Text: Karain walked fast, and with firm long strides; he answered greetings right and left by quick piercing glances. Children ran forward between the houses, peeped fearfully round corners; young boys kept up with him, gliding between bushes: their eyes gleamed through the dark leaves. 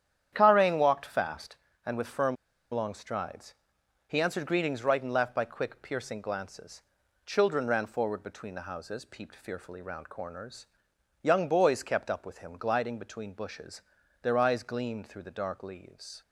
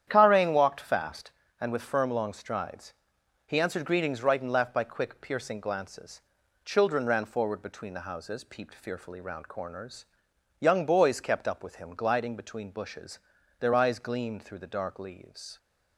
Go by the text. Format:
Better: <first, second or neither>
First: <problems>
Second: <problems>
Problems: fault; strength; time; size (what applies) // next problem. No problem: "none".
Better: second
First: starts louder than the rest; strong; until 1.3 s; 9.5 dB // pauses between "firm" and "long"; at 2.3 s; 0.37 s long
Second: starts louder than the rest; strong; until 1.0 s; 9.5 dB